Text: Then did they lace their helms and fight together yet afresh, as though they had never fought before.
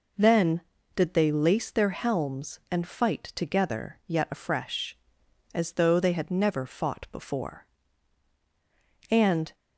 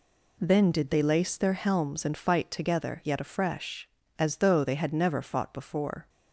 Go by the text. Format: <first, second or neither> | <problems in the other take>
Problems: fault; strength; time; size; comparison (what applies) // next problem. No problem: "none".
second | goes on to say "And"; slight; from 9.0 s on; 0.44 s long